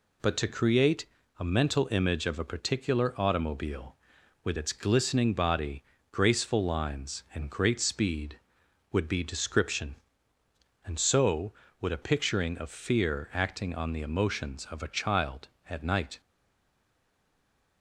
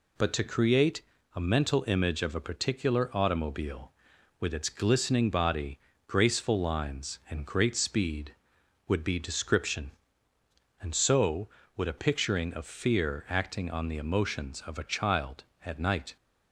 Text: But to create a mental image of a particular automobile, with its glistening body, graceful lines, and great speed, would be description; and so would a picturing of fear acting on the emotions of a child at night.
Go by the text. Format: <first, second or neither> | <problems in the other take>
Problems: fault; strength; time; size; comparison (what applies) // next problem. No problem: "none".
second | pauses between "create" and "a"; slight; at 1.0 s; 0.34 s long; slight in the second // stays silent after the last word; noticeable; from 16.2 s on; 1.6 s long